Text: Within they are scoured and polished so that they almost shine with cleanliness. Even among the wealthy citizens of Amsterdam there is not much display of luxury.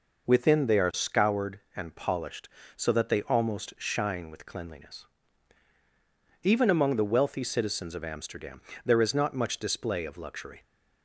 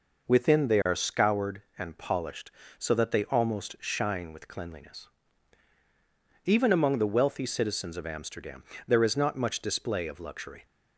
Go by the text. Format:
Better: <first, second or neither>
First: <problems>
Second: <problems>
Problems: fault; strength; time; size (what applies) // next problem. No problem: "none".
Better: neither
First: pauses between "Amsterdam" and "there"; slight; at 8.6 s; 0.24 s long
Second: pauses between "Amsterdam" and "there"; slight; at 8.6 s; 0.24 s long